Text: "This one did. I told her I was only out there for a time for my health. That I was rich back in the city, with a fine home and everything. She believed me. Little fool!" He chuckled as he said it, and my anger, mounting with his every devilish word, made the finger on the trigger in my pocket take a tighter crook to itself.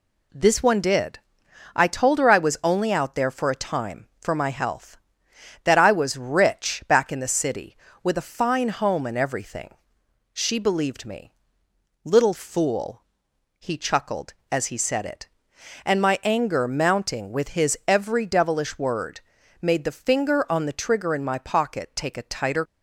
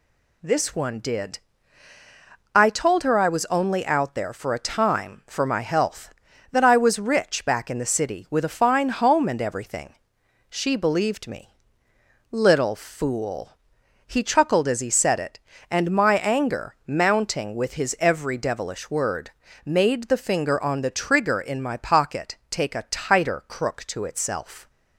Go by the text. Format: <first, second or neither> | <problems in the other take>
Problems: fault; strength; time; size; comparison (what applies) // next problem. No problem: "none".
second | stops before "crook to itself"; at 22.6 s